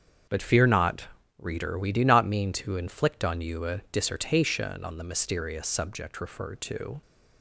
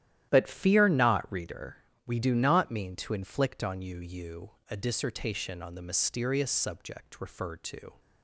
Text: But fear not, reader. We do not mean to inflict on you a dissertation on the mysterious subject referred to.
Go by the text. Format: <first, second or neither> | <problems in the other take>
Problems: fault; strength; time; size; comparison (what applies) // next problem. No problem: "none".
first | starts louder than the rest; strong; until 1.3 s; 12 dB; strong in the first // says "you" twice; at 3.9 s